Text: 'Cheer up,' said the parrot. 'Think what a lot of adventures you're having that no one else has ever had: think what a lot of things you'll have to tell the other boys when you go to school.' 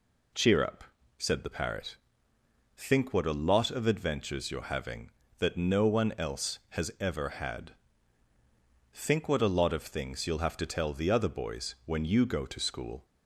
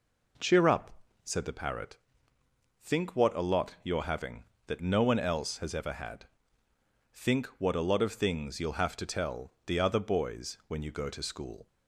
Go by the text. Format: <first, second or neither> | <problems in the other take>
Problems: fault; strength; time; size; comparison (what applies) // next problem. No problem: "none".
first | skips "of adventures"; at 3.7 s